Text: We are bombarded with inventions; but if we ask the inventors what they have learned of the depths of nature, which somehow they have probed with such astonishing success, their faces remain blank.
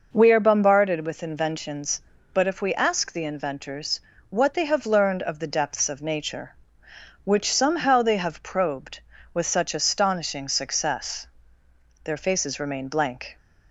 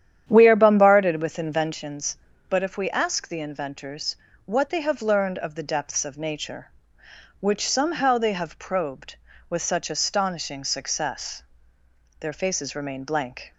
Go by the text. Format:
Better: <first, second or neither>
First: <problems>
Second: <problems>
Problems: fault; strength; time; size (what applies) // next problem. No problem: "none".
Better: first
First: pauses between "inventors" and "what"; slight; at 4.0 s; 0.28 s long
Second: starts louder than the rest; strong; until 1.9 s; 10 dB // pauses between "inventors" and "what"; slight; at 4.1 s; 0.28 s long